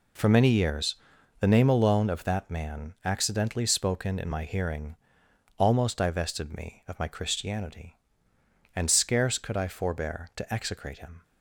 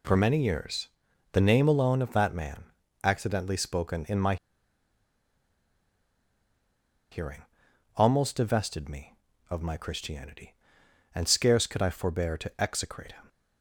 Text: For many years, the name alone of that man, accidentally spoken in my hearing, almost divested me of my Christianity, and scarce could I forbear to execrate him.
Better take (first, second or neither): first